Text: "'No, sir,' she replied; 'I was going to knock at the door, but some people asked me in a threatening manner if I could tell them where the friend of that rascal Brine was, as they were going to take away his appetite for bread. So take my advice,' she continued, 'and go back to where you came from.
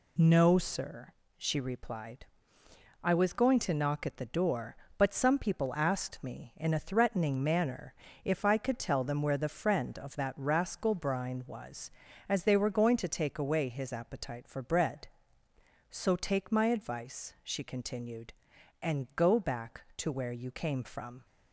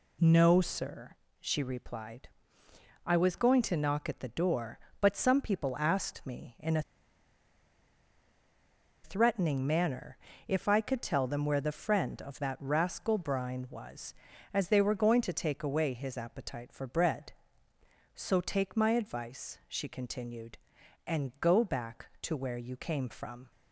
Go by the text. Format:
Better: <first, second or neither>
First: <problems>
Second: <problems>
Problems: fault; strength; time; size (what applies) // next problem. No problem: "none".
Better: first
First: pauses between "manner" and "if"; slight; at 7.9 s; 0.32 s long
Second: pauses between "a" and "threatening"; strong; at 6.8 s; 2.2 s long // pauses between "manner" and "if"; slight; at 10.1 s; 0.32 s long